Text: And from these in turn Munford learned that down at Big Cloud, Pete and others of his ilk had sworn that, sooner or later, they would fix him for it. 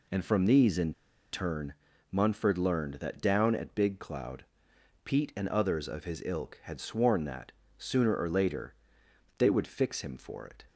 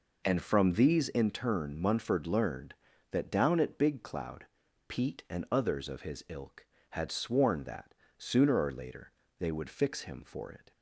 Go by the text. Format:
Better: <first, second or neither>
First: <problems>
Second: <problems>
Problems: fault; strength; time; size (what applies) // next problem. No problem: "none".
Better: second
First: pauses between "in" and "turn"; at 0.9 s; 0.39 s long // pauses between "turn" and "Munford"; at 1.7 s; 0.38 s long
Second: none